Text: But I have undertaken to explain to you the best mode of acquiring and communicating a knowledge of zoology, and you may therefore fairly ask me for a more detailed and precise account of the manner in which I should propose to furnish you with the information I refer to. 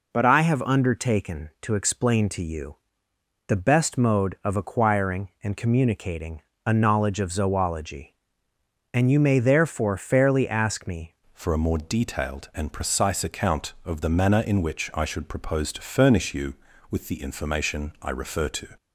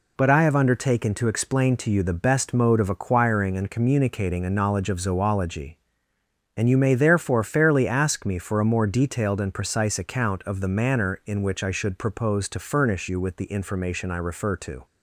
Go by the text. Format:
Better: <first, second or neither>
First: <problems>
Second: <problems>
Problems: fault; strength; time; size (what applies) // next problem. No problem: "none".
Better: second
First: pauses between "you" and "the"; noticeable; at 2.7 s; 0.72 s long // pauses between "communicating" and "a"; slight; at 6.4 s; 0.24 s long // changes voice at "for"; from 11.3 s on; 7.3 s long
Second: none